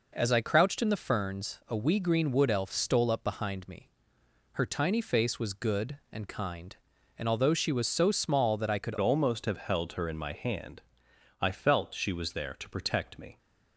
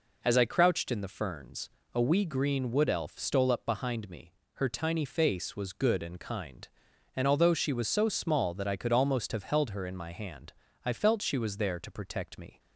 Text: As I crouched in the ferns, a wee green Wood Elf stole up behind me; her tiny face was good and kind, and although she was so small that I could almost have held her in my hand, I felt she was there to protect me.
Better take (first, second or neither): second